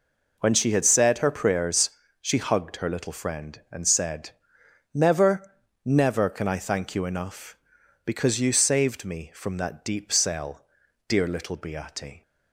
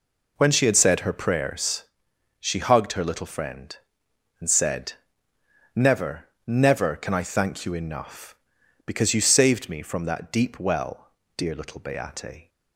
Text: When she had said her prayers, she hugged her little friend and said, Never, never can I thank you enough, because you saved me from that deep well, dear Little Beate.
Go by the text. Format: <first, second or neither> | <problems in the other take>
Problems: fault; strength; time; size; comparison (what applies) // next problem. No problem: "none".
second | says "cell" for "well"; at 10.1 s